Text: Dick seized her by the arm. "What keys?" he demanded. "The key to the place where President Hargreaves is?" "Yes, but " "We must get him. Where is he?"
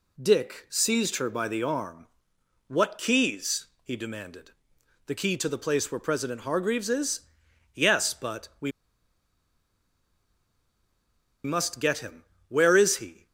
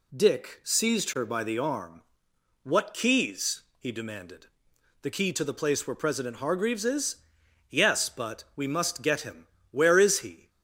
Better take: second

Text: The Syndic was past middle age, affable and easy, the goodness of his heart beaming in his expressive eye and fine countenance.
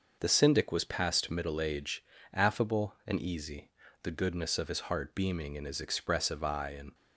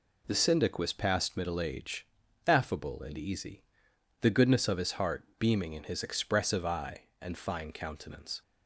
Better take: second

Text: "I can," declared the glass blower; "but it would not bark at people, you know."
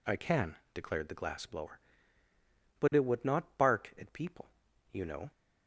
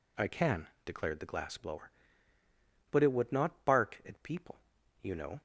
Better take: neither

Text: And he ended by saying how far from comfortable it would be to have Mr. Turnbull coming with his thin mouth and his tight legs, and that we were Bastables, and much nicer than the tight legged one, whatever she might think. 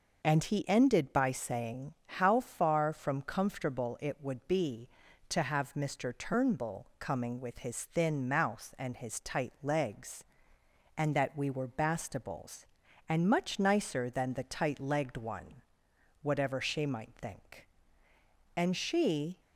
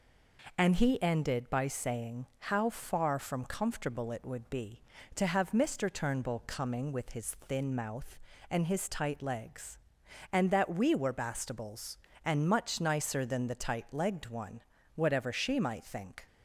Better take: second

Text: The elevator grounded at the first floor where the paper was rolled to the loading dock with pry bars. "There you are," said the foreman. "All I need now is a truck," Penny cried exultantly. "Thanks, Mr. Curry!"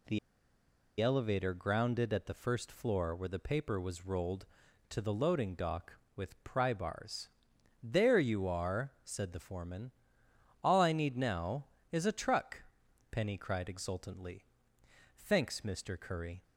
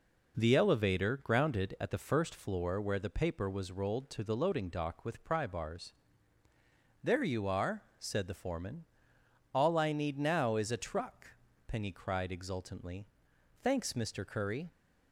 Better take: second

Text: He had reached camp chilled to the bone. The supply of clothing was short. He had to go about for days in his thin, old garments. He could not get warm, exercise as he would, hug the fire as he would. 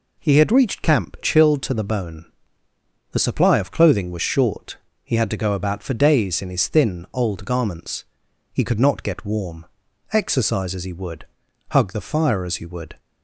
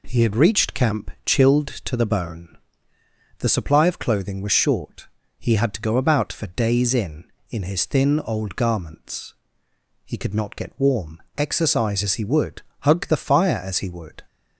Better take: first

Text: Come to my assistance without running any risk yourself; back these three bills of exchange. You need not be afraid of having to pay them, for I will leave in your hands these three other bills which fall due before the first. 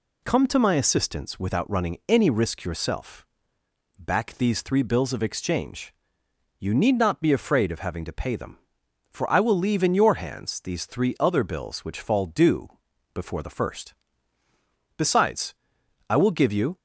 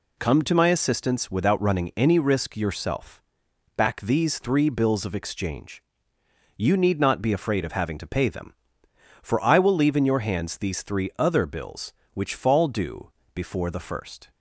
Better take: second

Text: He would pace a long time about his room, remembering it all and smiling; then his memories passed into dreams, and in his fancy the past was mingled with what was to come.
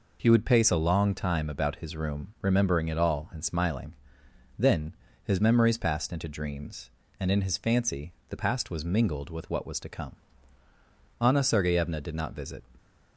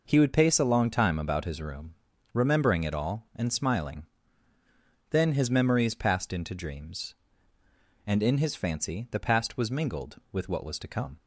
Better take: second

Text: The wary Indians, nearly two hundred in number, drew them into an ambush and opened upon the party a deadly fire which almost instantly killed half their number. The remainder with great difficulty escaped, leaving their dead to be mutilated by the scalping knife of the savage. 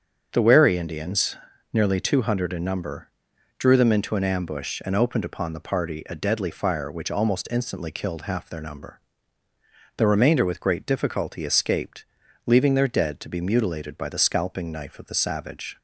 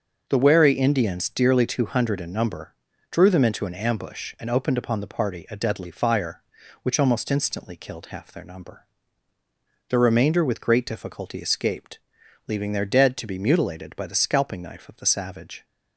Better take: first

